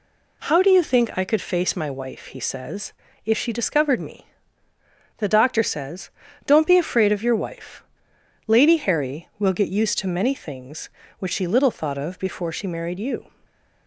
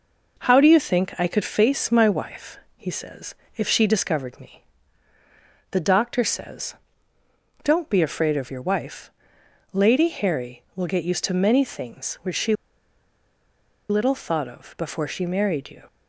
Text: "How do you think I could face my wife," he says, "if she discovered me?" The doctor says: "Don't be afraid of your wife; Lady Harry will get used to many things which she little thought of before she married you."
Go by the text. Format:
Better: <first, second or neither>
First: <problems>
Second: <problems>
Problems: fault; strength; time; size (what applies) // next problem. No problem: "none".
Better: first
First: none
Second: pauses between "she" and "little"; strong; at 12.5 s; 1.3 s long